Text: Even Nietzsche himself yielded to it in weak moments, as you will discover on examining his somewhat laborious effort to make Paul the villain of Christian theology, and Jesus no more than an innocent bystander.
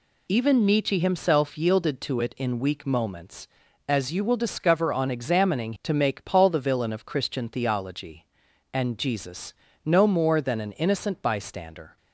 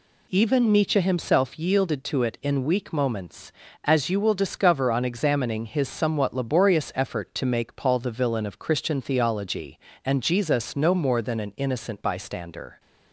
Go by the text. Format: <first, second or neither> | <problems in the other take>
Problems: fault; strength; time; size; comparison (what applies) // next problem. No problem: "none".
second | skips "his somewhat laborious effort"; at 5.7 s // pauses between "Jesus" and "no"; slight; at 9.5 s; 0.32 s long